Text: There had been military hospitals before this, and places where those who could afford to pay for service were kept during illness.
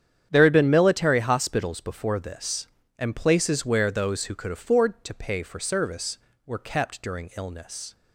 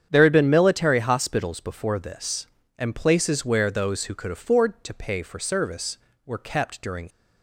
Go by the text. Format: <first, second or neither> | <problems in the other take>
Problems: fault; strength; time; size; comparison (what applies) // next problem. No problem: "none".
first | starts louder than the rest; strong; until 1.1 s; 8.5 dB; strong in the first // stops before "illness"; at 7.1 s